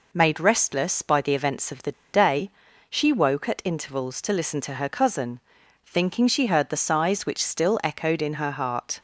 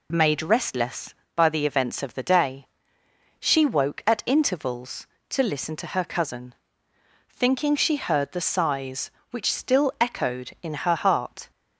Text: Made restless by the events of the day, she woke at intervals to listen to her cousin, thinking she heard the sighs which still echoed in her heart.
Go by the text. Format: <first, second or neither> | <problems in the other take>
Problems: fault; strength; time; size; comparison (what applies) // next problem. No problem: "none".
second | pauses between "the" and "day"; slight; at 1.9 s; 0.20 s long